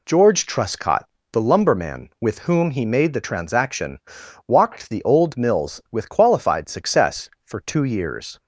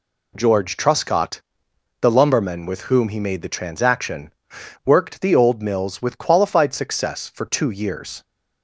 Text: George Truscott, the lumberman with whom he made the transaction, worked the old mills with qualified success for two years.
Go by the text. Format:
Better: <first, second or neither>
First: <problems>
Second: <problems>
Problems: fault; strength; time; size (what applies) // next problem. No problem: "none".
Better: second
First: says "walked" for "worked"; at 4.4 s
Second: none